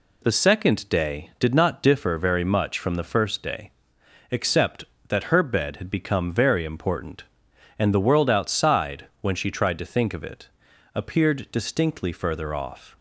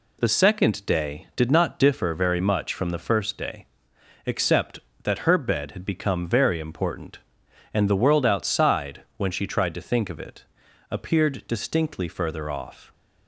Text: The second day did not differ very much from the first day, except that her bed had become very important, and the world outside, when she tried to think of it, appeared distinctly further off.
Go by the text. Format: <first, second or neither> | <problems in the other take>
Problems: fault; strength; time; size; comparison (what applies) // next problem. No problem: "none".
neither | none